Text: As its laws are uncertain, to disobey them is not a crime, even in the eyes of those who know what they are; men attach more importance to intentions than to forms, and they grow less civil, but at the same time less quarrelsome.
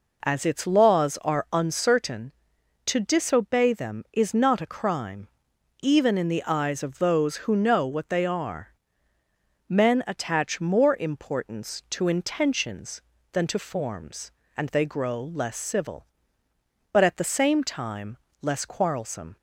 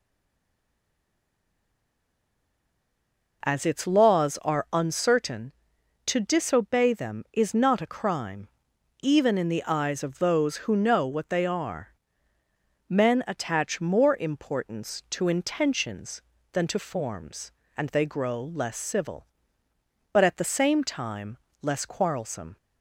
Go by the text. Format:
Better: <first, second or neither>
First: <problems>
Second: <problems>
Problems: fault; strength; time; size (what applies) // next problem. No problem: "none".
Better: first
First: pauses between "time" and "less"; slight; at 18.1 s; 0.24 s long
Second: stays silent before the first word; strong; until 3.4 s; 3.4 s long // pauses between "time" and "less"; slight; at 21.3 s; 0.24 s long